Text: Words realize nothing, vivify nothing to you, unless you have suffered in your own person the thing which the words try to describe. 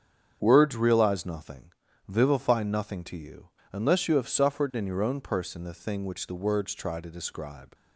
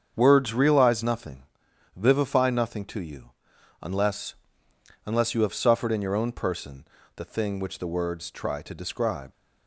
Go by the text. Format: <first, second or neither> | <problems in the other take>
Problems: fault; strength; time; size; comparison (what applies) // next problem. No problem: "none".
first | starts louder than the rest; strong; until 1.1 s; 7.5 dB; strong in the first // says "unless" twice; at 5.0 s // pauses between "person" and "the"; slight; at 6.8 s; 0.30 s long